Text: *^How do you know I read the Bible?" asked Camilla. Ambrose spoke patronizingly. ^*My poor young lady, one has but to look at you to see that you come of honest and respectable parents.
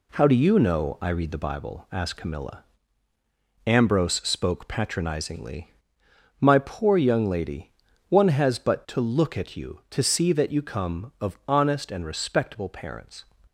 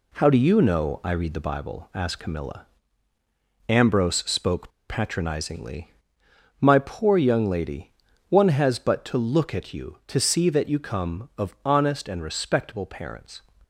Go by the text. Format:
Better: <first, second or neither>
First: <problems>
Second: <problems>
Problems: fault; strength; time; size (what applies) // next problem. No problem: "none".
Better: first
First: none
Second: pauses between "spoke" and "patronizingly"; slight; at 4.6 s; 0.19 s long